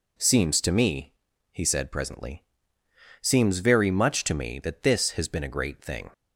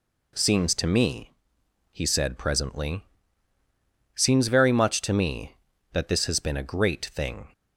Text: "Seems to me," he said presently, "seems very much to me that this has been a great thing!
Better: neither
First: none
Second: none

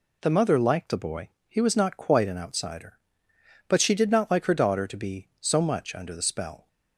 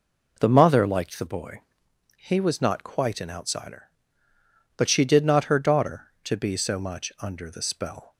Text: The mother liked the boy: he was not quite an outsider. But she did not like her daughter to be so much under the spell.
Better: first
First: none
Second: skips "like"; at 5.4 s

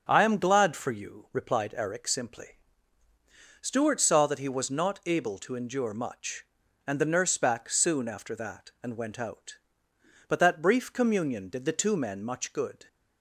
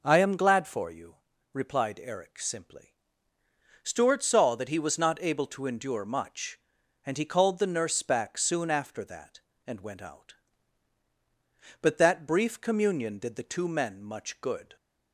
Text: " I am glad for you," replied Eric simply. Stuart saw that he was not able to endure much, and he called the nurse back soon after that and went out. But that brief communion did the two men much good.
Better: second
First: starts louder than the rest; noticeable; until 1.0 s; 6 dB // skips "he called"; at 6.9 s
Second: none

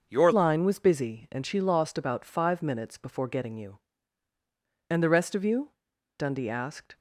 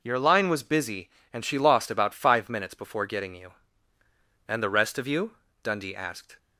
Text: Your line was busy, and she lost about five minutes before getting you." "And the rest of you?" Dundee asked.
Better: second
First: changes voice at "line"; from 0.3 s on; 6.6 s long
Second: none

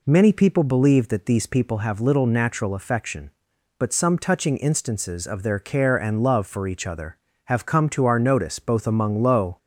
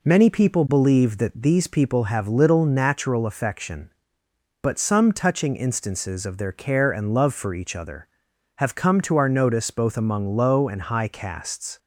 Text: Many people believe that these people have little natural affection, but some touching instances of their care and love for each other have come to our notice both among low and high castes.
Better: second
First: stops before "and high castes"; at 9.5 s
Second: none

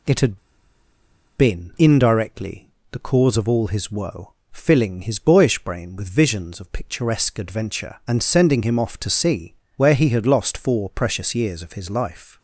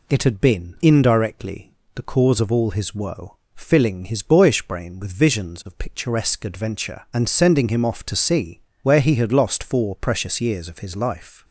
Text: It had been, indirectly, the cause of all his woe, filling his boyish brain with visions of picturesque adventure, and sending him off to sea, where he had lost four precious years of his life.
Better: second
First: pauses between "had" and "been"; at 0.3 s; 1.0 s long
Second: none

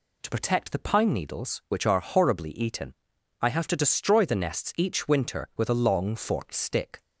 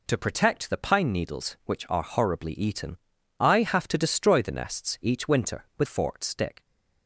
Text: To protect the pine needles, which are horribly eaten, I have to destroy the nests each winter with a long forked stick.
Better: first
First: none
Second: skips "a long"; at 5.8 s

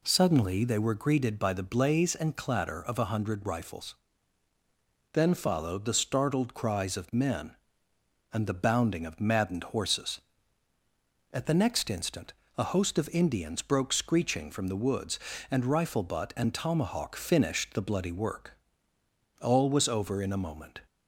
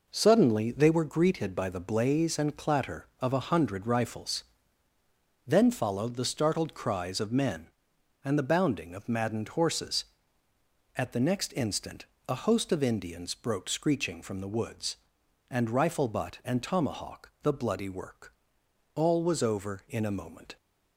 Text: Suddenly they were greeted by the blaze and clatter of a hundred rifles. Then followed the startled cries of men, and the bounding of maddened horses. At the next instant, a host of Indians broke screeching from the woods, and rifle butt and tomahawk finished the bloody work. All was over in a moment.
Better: first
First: none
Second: skips "finished"; at 17.3 s

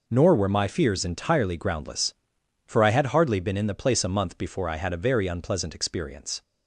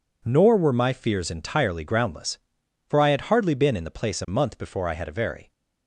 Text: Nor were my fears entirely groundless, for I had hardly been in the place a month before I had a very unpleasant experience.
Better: first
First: none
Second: stops before "unpleasant experience"; at 5.5 s

